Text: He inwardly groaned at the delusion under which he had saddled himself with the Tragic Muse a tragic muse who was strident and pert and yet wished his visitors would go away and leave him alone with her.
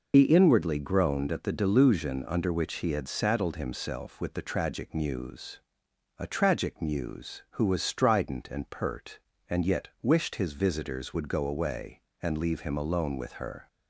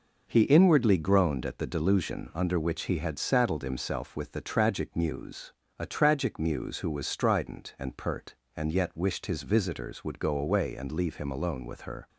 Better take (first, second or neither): second